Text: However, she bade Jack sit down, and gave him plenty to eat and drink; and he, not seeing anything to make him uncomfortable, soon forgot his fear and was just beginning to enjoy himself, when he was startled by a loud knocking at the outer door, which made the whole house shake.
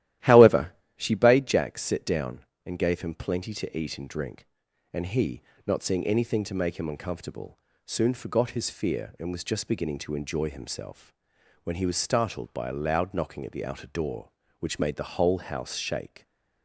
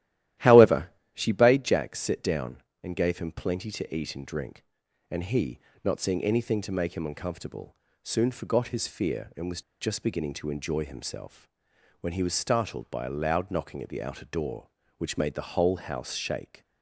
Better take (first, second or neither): first